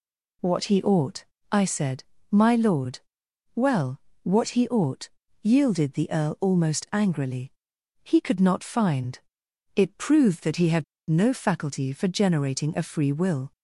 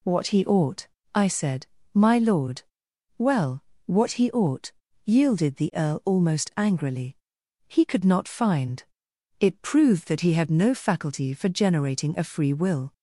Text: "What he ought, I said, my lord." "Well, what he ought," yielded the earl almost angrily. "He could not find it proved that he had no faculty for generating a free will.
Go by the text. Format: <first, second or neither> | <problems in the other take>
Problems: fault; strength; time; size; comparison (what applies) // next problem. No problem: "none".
second | pauses between "find" and "it"; noticeable; at 9.1 s; 0.58 s long; noticeable in the second // pauses between "had" and "no"; slight; at 10.8 s; 0.25 s long